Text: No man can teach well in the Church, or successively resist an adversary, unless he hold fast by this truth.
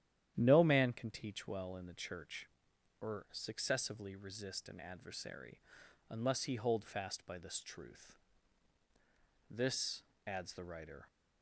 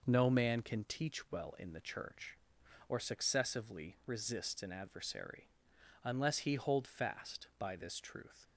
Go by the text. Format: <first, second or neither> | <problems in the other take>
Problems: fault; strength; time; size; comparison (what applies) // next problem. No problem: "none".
second | starts louder than the rest; strong; until 1.3 s; 11 dB // goes on to say "This adds the writer"; from 9.5 s on; 1.5 s long